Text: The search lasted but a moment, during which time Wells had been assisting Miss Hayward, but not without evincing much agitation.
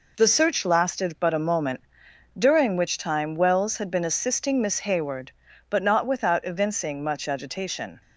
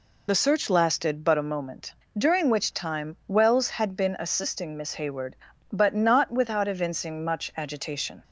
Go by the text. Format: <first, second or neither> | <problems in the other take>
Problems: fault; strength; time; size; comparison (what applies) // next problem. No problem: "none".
first | loses the start of "The"; at 0.2 s; 45 ms